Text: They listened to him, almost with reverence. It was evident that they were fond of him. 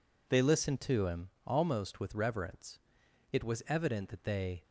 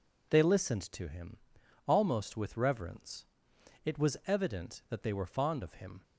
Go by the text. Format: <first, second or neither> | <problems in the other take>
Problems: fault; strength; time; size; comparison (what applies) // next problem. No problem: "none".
second | stops before "were fond of him"; at 4.6 s